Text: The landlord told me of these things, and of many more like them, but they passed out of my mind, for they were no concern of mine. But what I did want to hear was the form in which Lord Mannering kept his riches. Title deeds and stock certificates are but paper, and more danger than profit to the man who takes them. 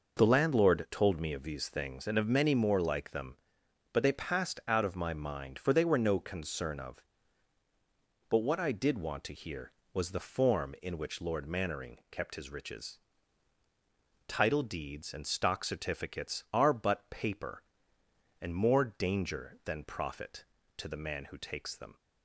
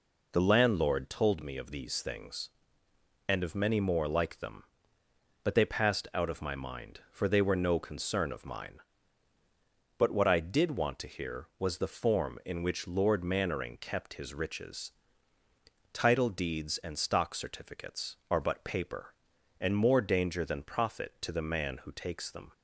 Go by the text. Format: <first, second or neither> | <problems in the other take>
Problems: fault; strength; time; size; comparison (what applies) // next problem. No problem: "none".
second | skips "mine"; at 7.6 s